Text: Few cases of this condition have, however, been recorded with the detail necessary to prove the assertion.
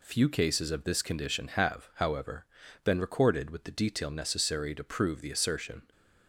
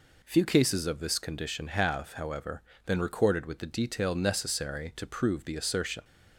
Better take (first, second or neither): neither